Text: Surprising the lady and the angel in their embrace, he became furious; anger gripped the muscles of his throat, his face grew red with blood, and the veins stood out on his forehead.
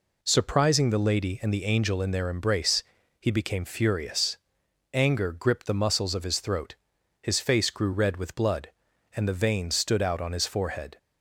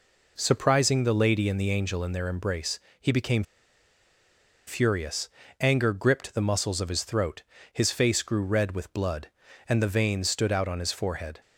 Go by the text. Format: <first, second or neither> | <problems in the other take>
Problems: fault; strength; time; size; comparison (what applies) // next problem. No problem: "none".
first | pauses between "became" and "furious"; at 3.4 s; 1.2 s long